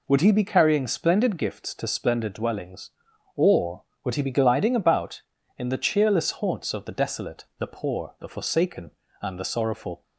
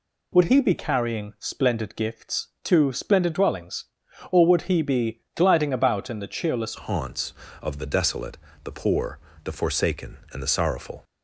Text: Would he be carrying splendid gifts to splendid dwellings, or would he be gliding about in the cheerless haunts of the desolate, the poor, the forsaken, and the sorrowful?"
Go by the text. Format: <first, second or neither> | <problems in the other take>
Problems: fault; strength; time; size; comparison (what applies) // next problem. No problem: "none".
first | changes voice at "haunts"; from 6.7 s on; 4.3 s long